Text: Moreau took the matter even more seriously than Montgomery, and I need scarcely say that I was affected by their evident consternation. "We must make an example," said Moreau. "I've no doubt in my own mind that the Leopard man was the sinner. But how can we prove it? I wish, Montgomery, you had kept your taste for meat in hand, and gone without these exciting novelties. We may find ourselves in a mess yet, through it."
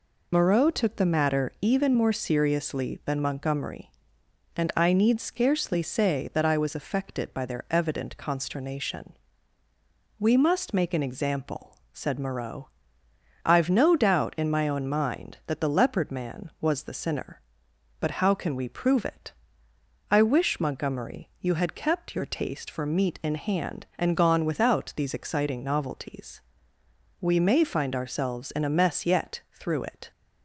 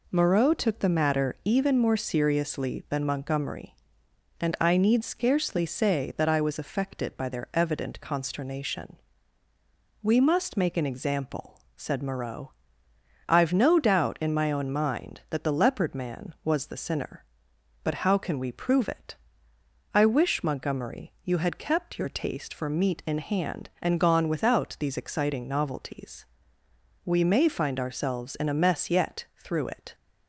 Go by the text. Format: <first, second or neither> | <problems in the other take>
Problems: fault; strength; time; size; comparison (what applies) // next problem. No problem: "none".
second | loses the start of "Moreau"; at 0.3 s; 95 ms